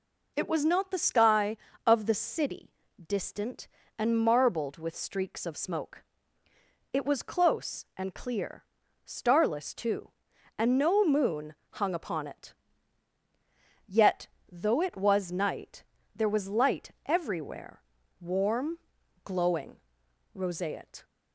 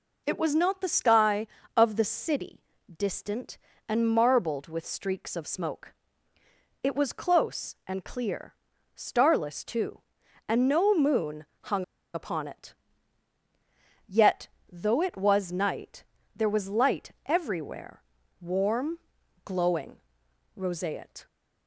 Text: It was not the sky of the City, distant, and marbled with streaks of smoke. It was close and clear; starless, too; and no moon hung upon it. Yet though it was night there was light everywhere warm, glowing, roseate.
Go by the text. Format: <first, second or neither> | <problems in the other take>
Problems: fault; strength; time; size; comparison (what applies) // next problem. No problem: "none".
first | pauses between "moon" and "hung"; slight; at 11.4 s; 0.20 s long; slight in the first // pauses between "hung" and "upon"; slight; at 11.8 s; 0.30 s long // pauses between "Yet" and "though"; slight; at 14.4 s; 0.26 s long; slight in the first // pauses between "night" and "there"; slight; at 16.0 s; 0.32 s long; slight in the first // pauses between "light" and "everywhere"; slight; at 17.0 s; 0.16 s long; slight in the first // pauses between "everywhere" and "warm"; slight; at 18.0 s; 0.36 s long; slight in the first